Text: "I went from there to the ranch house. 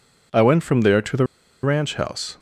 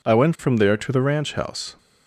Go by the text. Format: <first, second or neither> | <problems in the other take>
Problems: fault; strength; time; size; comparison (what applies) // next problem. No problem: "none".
second | pauses between "the" and "ranch"; at 1.2 s; 0.37 s long